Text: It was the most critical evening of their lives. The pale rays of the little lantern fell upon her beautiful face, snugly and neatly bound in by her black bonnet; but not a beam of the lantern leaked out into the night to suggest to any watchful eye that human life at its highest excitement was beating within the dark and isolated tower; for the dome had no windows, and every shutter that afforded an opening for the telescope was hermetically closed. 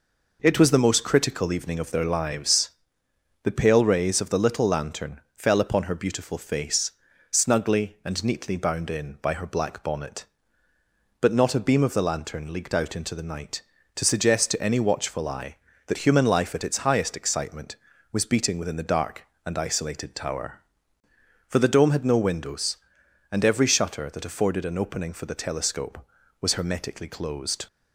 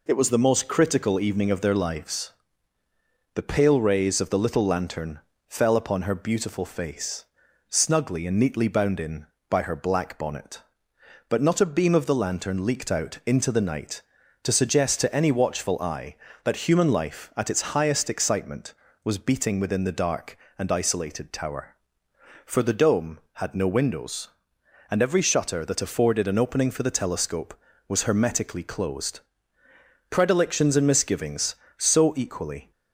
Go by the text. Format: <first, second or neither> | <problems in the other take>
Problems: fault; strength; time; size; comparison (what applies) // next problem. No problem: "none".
first | pauses between "lantern" and "fell"; slight; at 5.1 s; 0.30 s long; slight in the first // goes on to say "Predilections and misgivings so equally"; strong; from 30.0 s on; 2.6 s long